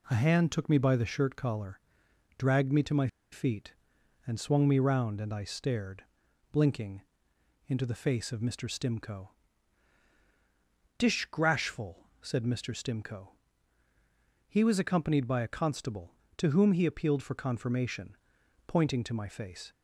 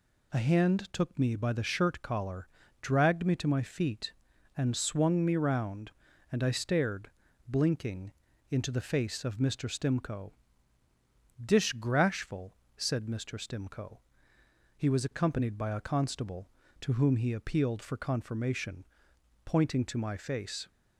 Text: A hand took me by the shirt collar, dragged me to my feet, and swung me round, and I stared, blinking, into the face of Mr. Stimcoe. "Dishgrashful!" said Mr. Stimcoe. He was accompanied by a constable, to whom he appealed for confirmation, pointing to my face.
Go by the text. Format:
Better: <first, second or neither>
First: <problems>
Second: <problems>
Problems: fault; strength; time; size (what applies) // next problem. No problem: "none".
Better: second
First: pauses between "my" and "feet"; slight; at 3.0 s; 0.25 s long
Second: none